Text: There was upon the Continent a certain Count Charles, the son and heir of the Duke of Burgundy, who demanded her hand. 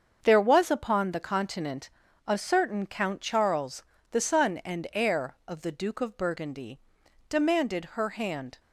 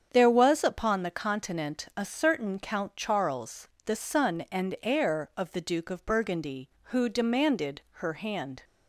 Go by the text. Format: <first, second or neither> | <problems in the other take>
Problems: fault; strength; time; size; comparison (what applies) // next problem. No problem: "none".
second | starts louder than the rest; until 1.2 s; 7 dB; strong in the second // pauses between "Continent" and "a"; at 1.8 s; 0.38 s long // skips "who"; at 7.0 s